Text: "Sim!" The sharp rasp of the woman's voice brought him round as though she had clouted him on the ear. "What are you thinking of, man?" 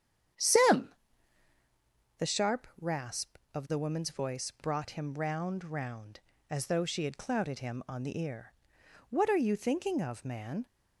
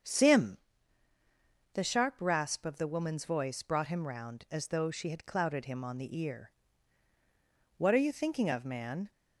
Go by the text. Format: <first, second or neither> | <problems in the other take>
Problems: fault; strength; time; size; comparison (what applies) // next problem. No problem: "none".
second | starts louder than the rest; strong; until 2.6 s; 9 dB; also in the second // says "round" twice; at 5.6 s